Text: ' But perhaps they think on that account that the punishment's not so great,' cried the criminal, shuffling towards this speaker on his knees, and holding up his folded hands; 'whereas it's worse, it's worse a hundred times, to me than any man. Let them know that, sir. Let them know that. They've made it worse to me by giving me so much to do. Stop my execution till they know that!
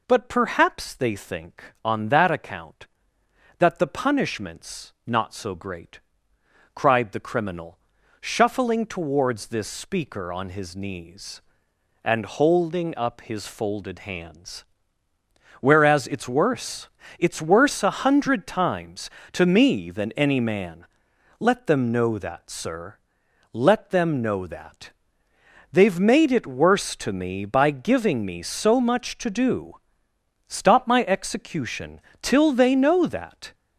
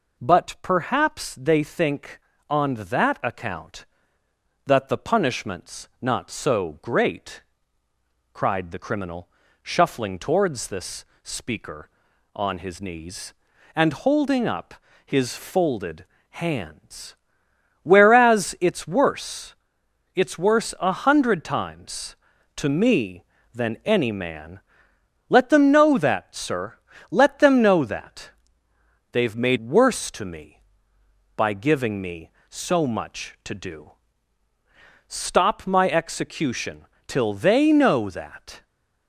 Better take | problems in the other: first | pauses between "this" and "speaker"; slight; at 11.0 s; 0.18 s long // pauses between "up" and "his"; slight; at 14.7 s; 0.32 s long // pauses between "folded" and "hands"; slight; at 16.0 s; 0.26 s long // skips "it"; at 29.5 s // pauses between "execution" and "till"; slight; at 36.8 s; 0.22 s long; slight in the first

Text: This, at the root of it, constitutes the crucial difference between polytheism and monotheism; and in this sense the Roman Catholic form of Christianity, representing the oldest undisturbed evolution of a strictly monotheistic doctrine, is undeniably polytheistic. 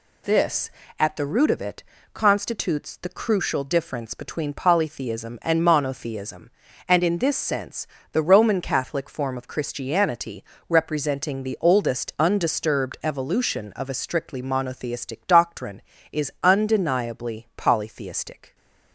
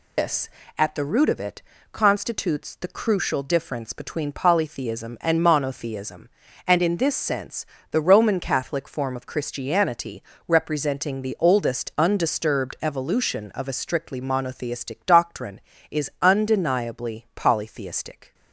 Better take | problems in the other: first | loses the start of "This"; at 0.1 s; 150 ms // pauses between "sense" and "the"; slight; at 7.6 s; 0.26 s long; slight in the first

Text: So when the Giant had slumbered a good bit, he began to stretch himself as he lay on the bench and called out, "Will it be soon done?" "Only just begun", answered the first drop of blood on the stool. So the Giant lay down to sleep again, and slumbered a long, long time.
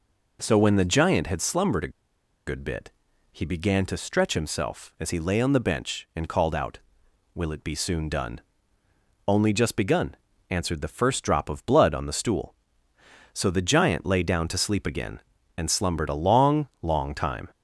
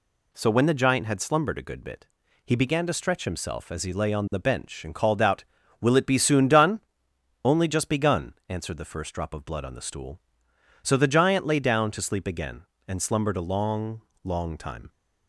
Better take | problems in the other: second | pauses between "a" and "good"; noticeable; at 1.9 s; 0.57 s long

